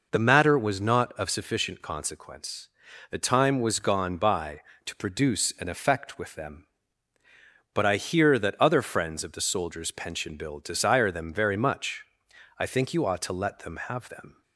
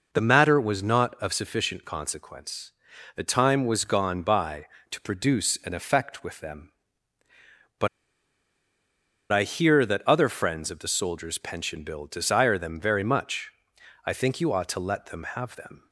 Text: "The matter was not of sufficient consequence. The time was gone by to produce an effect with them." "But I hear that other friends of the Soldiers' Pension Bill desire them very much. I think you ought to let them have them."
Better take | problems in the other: first | pauses between "But" and "I"; strong; at 7.8 s; 1.4 s long

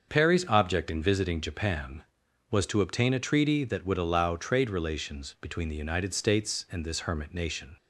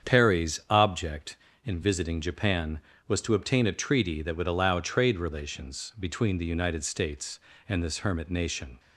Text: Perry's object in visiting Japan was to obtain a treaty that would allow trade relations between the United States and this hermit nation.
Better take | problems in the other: neither | starts louder than the rest; the same in both

